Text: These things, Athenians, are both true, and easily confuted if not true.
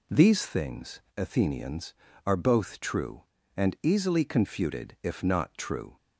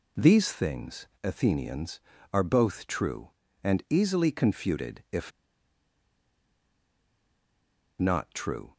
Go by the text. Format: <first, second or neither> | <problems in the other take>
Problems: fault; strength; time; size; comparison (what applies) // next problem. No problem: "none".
first | pauses between "if" and "not"; strong; at 5.3 s; 2.6 s long